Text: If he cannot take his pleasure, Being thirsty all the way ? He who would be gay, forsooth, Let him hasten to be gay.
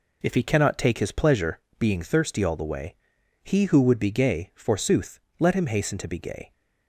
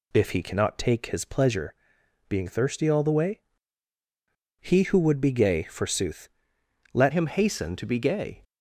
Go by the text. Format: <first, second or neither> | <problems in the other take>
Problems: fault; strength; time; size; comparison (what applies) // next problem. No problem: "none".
first | changes voice at "him"; from 7.1 s on; 1.3 s long